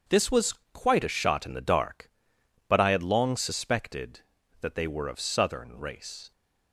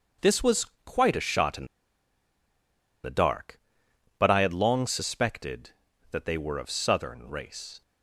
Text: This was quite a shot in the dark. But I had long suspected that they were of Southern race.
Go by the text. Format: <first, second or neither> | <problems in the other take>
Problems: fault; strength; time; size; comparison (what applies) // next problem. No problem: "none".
first | starts louder than the rest; until 1.3 s; 7 dB; also in the first // pauses between "was" and "quite"; slight; at 0.6 s; 0.18 s long; slight in the first // pauses between "in" and "the"; strong; at 1.6 s; 1.3 s long